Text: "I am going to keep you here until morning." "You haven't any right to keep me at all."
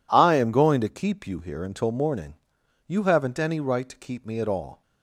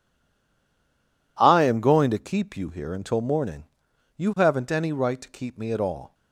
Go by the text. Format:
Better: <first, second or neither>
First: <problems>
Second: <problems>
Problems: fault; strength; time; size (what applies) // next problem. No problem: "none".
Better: first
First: none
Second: stays silent before the first word; noticeable; until 1.3 s; 1.3 s long